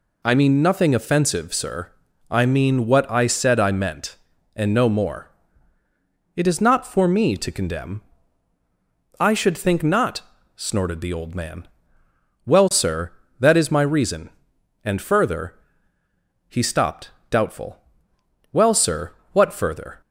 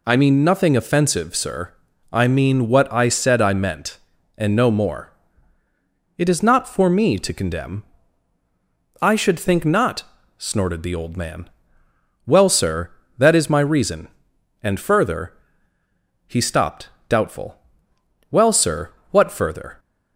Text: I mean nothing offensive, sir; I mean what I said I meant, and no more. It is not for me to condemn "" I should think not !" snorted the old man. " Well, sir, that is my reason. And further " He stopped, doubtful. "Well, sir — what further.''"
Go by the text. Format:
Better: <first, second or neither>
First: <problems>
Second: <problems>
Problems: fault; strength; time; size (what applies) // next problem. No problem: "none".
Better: neither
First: none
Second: none